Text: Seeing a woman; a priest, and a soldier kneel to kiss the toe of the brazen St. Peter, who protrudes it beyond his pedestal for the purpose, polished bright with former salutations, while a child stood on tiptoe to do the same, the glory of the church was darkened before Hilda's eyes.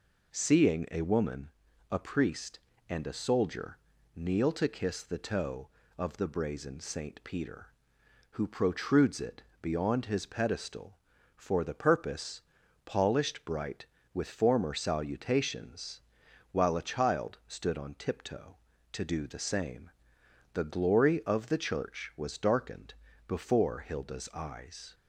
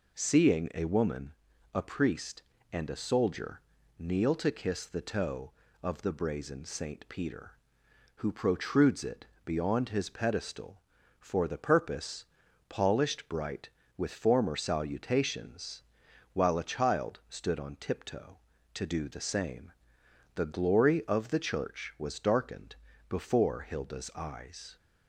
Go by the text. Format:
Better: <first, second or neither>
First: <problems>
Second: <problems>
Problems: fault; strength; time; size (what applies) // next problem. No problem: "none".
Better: neither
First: pauses between "soldier" and "kneel"; slight; at 3.7 s; 0.36 s long // pauses between "it" and "beyond"; slight; at 9.4 s; 0.22 s long // pauses between "darkened" and "before"; slight; at 22.9 s; 0.34 s long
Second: pauses between "soldier" and "kneel"; slight; at 3.6 s; 0.36 s long // pauses between "it" and "beyond"; slight; at 9.2 s; 0.22 s long // pauses between "darkened" and "before"; slight; at 22.7 s; 0.34 s long